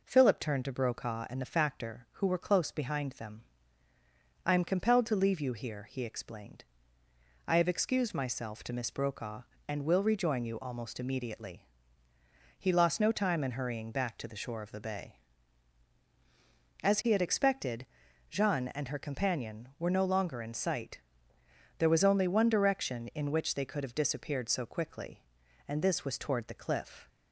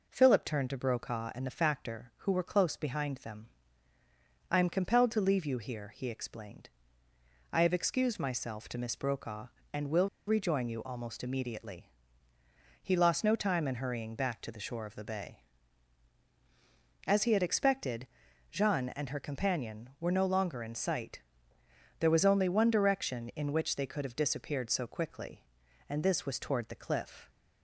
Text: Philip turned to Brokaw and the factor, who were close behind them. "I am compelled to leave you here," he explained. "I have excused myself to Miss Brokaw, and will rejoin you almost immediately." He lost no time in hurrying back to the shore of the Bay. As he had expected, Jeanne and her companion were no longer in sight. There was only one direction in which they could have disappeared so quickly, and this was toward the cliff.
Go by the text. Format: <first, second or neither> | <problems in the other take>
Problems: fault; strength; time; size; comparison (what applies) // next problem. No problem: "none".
first | pauses between "will" and "rejoin"; slight; at 10.0 s; 0.18 s long